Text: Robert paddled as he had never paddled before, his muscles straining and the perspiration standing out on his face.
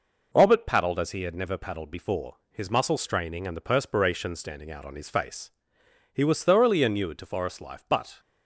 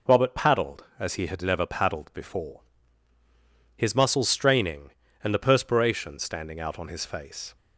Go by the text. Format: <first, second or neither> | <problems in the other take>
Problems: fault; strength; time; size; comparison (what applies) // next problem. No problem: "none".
second | goes on to say "He was thoroughly inured to forest life but"; strong; from 6.1 s on; 2.0 s long